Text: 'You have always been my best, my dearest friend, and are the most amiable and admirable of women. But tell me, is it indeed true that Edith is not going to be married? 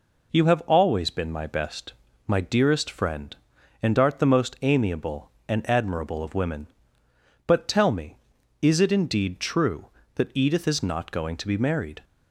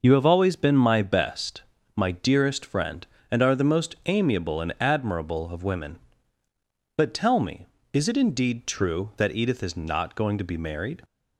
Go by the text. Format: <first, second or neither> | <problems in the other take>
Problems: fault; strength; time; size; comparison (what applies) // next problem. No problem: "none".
second | says "art" for "are"; at 3.9 s